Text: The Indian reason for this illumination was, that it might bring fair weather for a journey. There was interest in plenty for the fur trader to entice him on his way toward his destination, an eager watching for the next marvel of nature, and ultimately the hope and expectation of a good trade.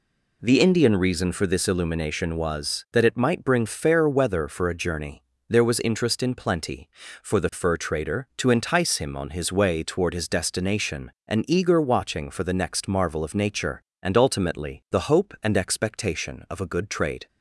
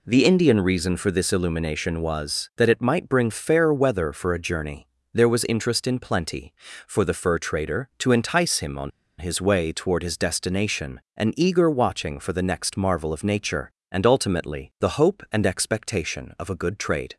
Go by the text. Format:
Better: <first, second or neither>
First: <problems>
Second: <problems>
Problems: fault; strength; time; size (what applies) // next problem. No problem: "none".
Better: first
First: none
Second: pauses between "on" and "his"; slight; at 8.9 s; 0.27 s long